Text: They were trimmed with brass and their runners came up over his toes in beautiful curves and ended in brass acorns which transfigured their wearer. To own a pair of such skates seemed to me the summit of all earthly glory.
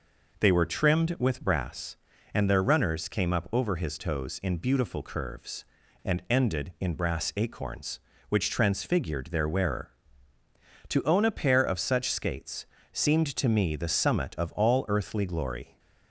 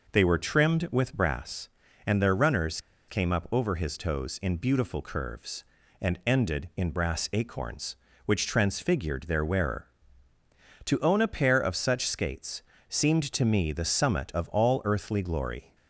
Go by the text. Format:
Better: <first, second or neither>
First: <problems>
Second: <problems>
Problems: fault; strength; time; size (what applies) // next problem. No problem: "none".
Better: first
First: pauses between "skates" and "seemed"; slight; at 12.6 s; 0.26 s long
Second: pauses between "runners" and "came"; slight; at 2.8 s; 0.28 s long // pauses between "skates" and "seemed"; slight; at 12.6 s; 0.26 s long